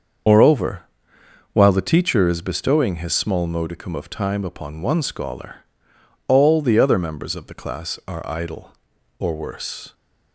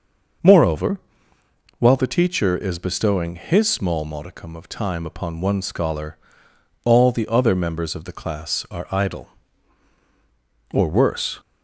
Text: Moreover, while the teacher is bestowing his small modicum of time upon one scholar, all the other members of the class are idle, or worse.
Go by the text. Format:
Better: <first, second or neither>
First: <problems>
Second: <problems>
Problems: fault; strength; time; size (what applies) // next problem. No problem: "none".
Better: second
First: loses the start of "Moreover"; at 0.2 s; 85 ms // starts louder than the rest; until 1.9 s; 7 dB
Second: starts louder than the rest; until 2.2 s; 6 dB